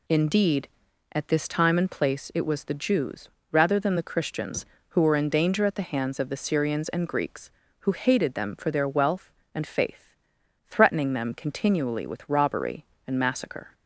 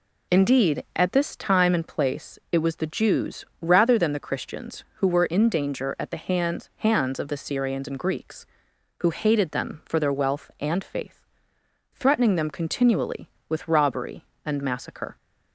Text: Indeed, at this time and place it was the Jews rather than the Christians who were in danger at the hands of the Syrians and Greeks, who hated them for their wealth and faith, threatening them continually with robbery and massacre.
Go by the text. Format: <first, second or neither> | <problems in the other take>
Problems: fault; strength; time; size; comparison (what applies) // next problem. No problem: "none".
first | pauses between "Jews" and "rather"; slight; at 3.4 s; 0.16 s long; slight in the first // says "hands" twice; at 6.7 s